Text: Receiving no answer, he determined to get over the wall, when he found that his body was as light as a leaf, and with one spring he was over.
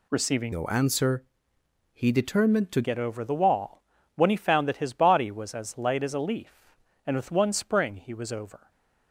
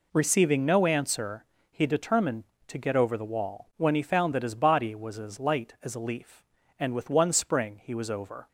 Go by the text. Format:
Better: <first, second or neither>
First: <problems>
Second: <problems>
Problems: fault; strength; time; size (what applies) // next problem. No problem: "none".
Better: second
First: changes voice from "no" to "to"; from 0.5 to 2.8 s; 2.3 s long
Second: none